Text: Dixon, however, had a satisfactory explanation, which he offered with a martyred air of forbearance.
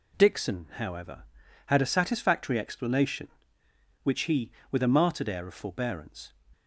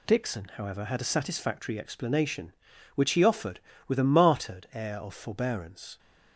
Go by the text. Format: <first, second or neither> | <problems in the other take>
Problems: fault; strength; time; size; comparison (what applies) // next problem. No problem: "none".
second | skips "offered"; at 4.6 s